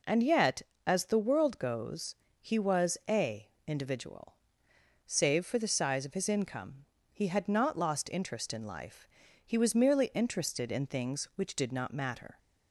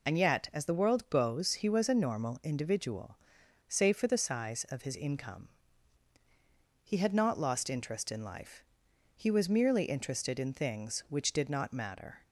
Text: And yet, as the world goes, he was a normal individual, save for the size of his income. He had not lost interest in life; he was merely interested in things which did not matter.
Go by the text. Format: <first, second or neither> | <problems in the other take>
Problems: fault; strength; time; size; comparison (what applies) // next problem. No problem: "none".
second | skips "normal"; at 3.5 s